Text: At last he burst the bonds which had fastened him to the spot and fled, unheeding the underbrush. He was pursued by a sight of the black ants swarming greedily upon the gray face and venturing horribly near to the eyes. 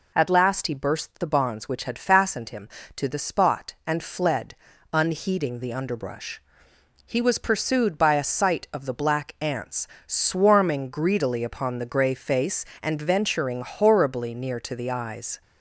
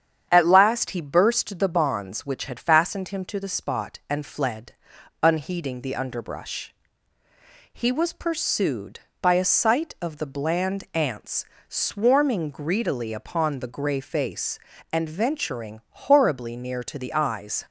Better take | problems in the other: first | starts louder than the rest; strong; until 1.3 s; 8.5 dB // says "bland" for "black"; at 10.2 s // pauses between "ants" and "swarming"; slight; at 11.4 s; 0.24 s long; slight in the first

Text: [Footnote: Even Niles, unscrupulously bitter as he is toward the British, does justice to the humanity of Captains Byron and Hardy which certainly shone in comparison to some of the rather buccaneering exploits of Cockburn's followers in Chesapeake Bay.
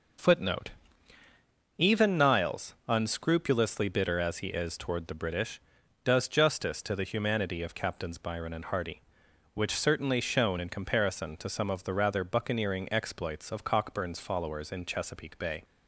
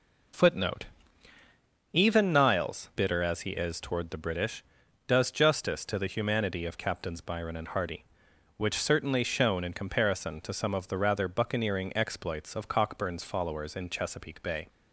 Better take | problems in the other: first | skips "unscrupulously"; at 2.9 s

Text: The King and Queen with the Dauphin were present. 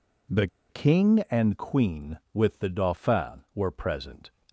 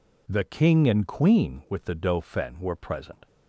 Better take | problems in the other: second | pauses between "The" and "King"; slight; at 0.4 s; 0.24 s long

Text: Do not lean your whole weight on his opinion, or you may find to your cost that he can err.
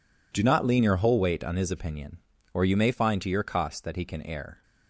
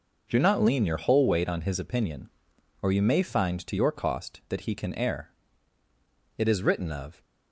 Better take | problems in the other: first | goes on to say "It is written of"; noticeable; from 6.3 s on; 0.86 s long

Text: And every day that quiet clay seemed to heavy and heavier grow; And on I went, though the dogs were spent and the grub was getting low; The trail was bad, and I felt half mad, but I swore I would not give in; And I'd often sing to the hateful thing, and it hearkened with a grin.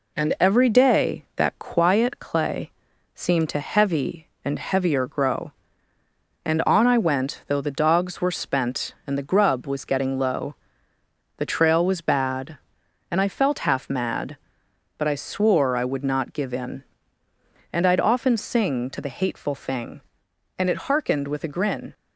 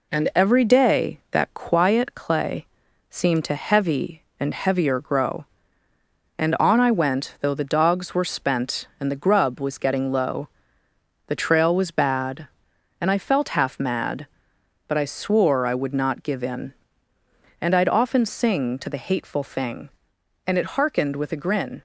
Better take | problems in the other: neither | pauses between "clay" and "seemed"; the same in both

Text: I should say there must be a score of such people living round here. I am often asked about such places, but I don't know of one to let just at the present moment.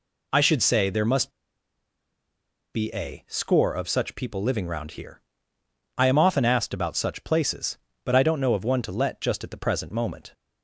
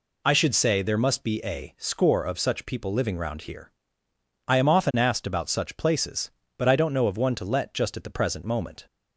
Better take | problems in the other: second | pauses between "must" and "be"; strong; at 1.3 s; 1.4 s long

